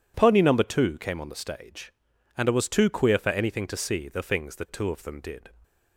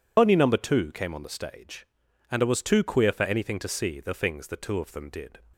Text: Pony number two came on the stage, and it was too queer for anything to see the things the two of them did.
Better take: first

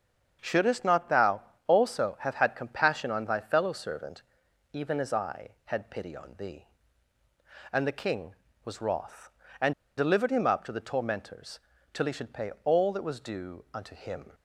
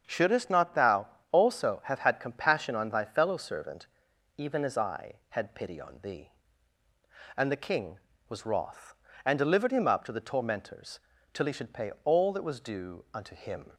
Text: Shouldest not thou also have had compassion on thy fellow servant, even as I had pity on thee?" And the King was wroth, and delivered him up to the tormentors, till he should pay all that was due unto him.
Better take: second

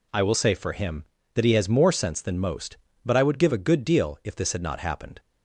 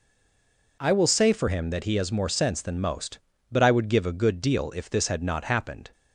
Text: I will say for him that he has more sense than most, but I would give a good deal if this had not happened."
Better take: first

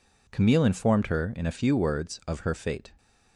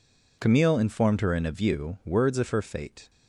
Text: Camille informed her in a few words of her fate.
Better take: first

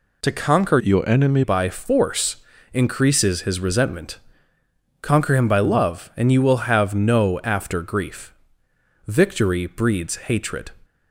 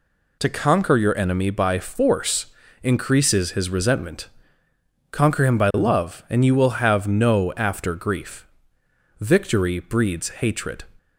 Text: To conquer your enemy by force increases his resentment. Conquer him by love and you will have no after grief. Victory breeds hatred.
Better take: second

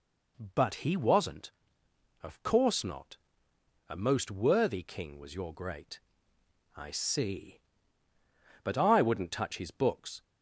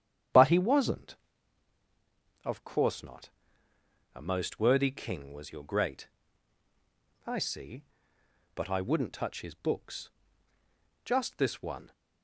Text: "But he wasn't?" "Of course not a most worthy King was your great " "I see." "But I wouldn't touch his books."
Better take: first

